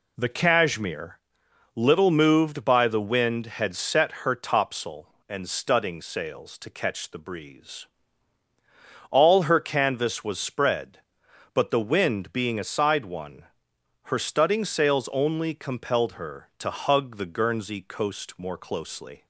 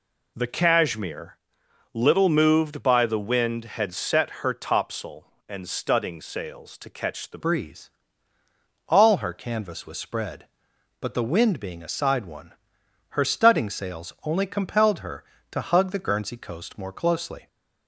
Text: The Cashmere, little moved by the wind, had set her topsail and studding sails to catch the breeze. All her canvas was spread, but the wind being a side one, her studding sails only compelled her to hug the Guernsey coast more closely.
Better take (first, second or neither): first